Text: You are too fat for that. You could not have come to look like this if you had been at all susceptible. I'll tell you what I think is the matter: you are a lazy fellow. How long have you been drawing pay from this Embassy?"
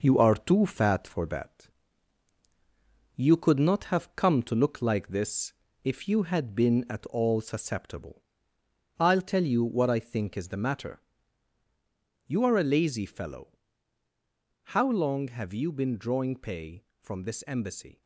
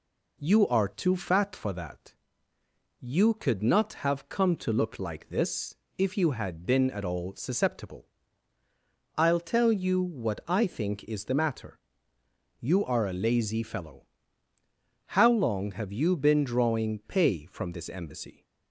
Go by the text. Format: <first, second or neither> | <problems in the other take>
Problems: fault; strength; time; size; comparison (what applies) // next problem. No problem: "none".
second | gets quieter; noticeable; throughout; 4.5 dB // pauses between "this" and "if"; slight; at 5.5 s; 0.30 s long; slight in the second